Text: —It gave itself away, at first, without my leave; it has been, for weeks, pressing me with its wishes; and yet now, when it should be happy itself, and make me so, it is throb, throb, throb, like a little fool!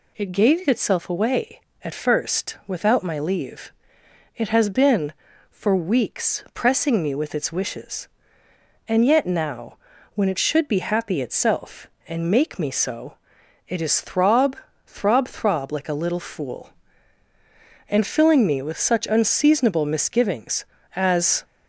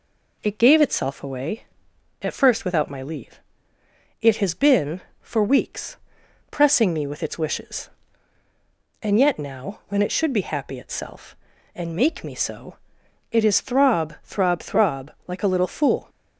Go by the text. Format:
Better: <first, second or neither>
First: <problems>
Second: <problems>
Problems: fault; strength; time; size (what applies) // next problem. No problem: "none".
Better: second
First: goes on to say "and filling me with such unseasonable misgivings as"; strong; from 17.8 s on; 3.5 s long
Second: none